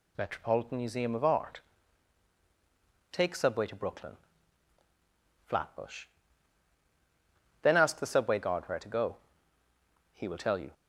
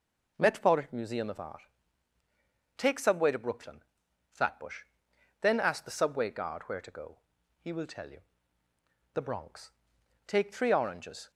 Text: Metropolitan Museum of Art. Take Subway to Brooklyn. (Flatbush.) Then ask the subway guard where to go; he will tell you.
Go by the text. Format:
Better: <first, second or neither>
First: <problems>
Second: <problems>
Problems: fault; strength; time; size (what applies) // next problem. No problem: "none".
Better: first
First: none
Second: goes on to say "The Bronx Take three oranges"; strong; from 9.1 s on; 2.1 s long